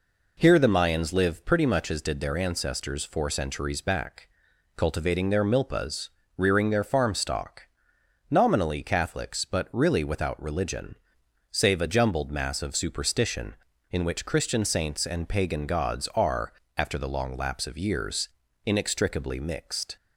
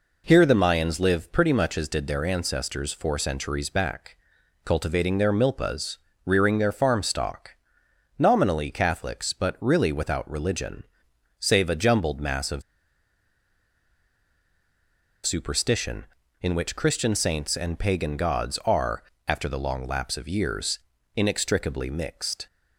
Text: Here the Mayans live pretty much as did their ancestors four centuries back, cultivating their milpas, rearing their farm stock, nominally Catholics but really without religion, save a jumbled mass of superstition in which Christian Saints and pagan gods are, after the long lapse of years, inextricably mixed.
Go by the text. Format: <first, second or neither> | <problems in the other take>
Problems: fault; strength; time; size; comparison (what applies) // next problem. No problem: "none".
first | pauses between "of" and "superstition"; strong; at 12.6 s; 2.6 s long